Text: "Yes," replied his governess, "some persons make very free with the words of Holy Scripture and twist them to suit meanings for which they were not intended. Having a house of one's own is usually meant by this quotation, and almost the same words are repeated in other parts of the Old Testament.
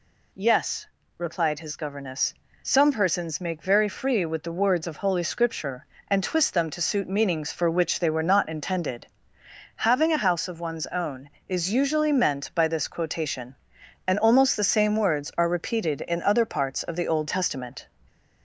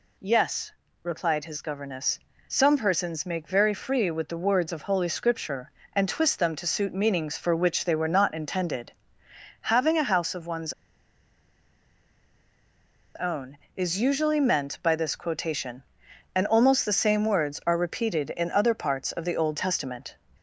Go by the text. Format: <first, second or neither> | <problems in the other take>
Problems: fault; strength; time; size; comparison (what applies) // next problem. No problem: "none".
first | pauses between "one's" and "own"; strong; at 10.7 s; 2.4 s long